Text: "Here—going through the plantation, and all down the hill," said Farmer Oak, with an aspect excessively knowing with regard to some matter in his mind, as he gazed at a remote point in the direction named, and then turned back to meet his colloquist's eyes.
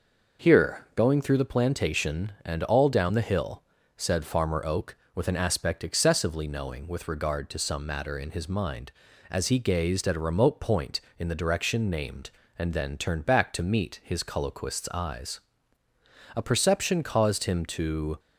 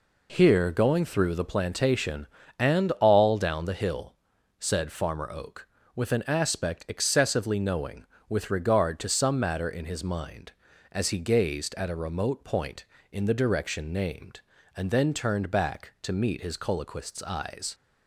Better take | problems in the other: second | goes on to say "A perception caused him to"; strong; from 16.3 s on; 1.8 s long

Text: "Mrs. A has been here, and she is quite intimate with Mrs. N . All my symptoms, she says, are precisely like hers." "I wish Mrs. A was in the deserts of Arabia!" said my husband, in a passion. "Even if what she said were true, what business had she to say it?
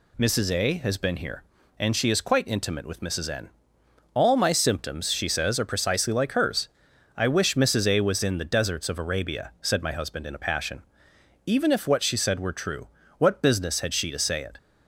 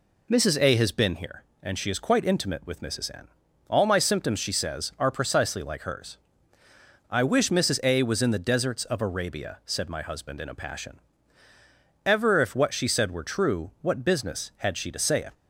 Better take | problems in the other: first | says "Ever" for "Even"; at 12.0 s

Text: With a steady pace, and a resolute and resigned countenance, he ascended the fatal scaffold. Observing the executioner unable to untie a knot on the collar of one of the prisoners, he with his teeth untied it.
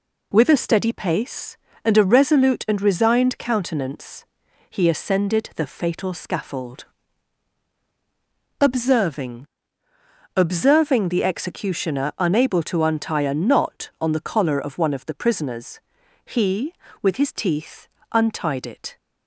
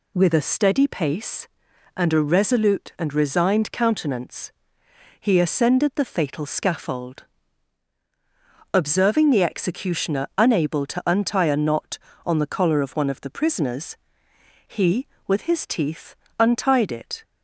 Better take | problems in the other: second | says "Observing" twice; at 10.3 s // pauses between "teeth" and "untied"; slight; at 17.8 s; 0.24 s long; slight in the second

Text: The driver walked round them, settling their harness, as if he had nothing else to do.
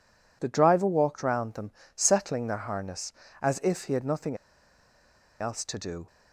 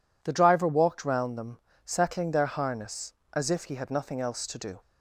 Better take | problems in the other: second | pauses between "nothing" and "else"; at 4.3 s; 1.0 s long

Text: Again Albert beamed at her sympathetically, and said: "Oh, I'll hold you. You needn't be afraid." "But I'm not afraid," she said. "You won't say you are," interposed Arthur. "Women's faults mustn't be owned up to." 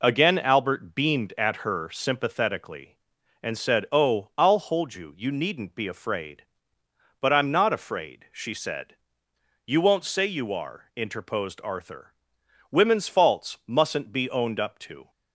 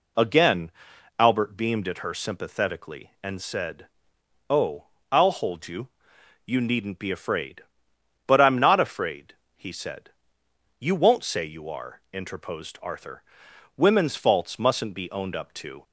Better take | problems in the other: first | pauses between "Again" and "Albert"; noticeable; at 0.7 s; 0.48 s long // says "he" for "she"; at 9.5 s

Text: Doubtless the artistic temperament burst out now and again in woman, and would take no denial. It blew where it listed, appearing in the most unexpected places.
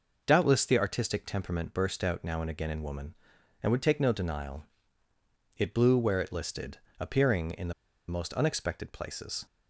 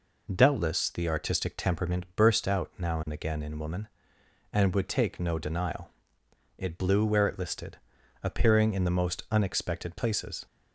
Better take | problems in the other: second | pauses between "the" and "most"; at 7.7 s; 0.36 s long

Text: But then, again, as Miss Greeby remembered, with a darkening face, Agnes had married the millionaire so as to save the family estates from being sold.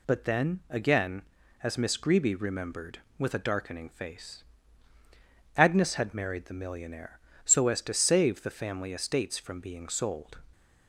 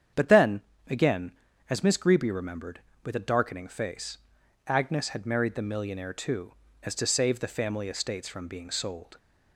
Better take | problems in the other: first | starts louder than the rest; strong; until 1.7 s; 8.5 dB // says "too" for "so"; at 6.1 s

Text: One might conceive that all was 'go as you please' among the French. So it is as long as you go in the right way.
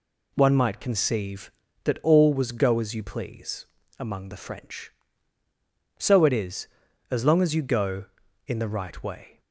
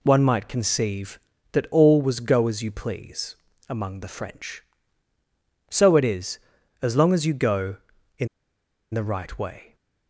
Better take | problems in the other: first | pauses between "please" and "among"; slight; at 3.3 s; 0.32 s long; slight in the first // pauses between "in" and "the"; noticeable; at 8.2 s; 0.65 s long

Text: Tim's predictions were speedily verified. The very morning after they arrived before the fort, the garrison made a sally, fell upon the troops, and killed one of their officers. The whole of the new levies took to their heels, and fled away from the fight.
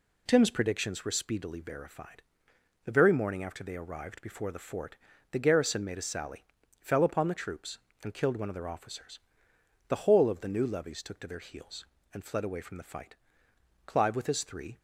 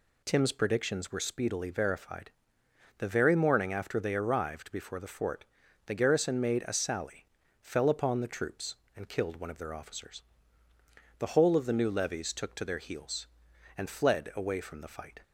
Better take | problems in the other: second | goes on to say "Clive with his three"; noticeable; from 13.8 s on; 0.94 s long

